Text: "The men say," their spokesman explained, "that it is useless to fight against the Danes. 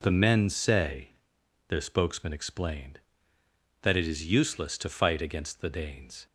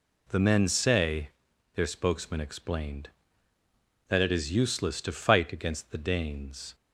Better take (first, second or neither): neither